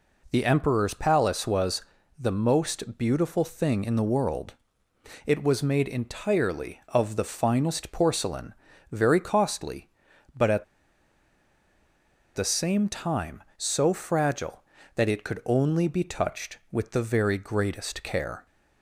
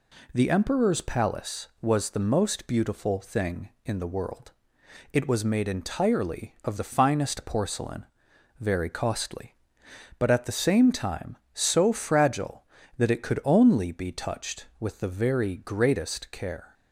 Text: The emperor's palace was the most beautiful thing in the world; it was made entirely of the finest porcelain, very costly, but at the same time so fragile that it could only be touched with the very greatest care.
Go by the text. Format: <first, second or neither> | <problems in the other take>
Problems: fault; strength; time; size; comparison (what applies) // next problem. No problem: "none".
second | pauses between "was" and "the"; slight; at 1.8 s; 0.36 s long // pauses between "at" and "the"; strong; at 10.6 s; 1.7 s long